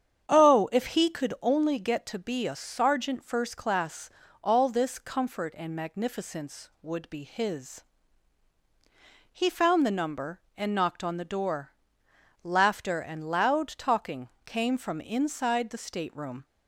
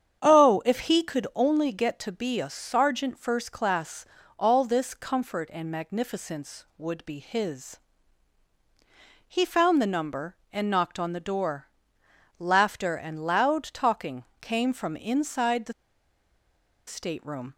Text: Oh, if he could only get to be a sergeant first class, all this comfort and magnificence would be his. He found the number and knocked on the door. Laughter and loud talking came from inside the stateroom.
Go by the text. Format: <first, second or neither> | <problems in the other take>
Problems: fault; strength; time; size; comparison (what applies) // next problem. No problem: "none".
first | starts louder than the rest; strong; until 1.2 s; 8.5 dB; strong in the first // pauses between "talking" and "came"; slight; at 14.2 s; 0.16 s long; slight in the first // pauses between "the" and "stateroom"; at 15.7 s; 1.1 s long